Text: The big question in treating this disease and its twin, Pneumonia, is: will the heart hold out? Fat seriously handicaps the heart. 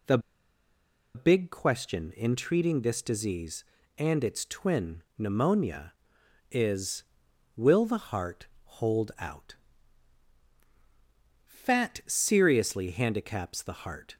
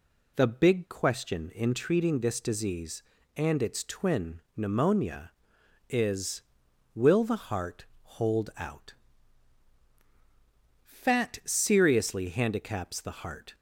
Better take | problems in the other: second | pauses between "The" and "big"; noticeable; at 0.1 s; 0.96 s long // pauses between "heart" and "hold"; slight; at 8.4 s; 0.16 s long; slight in the second

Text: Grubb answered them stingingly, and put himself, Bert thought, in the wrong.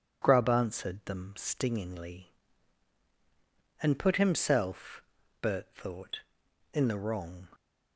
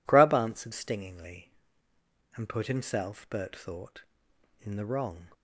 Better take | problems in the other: first | skips "them"; at 0.7 s

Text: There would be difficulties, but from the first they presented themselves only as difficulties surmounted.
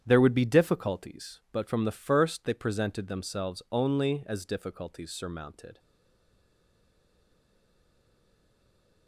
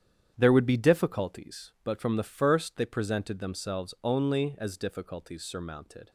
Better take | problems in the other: second | starts louder than the rest; strong; until 1.0 s; 9.5 dB; strong in the second // stays silent after the last word; strong; from 5.7 s on; 3.3 s long

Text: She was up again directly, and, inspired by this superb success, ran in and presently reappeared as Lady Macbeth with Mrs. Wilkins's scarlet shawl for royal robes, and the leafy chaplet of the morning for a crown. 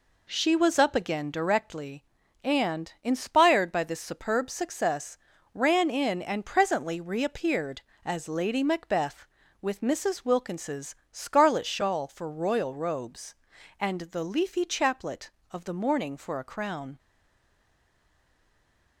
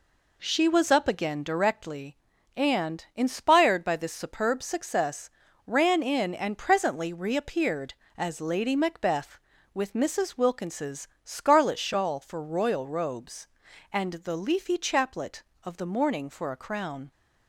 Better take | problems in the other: second | pauses between "Wilkins's" and "scarlet"; slight; at 10.9 s; 0.16 s long; slight in the second // stays silent after the last word; noticeable; from 16.9 s on; 2.1 s long

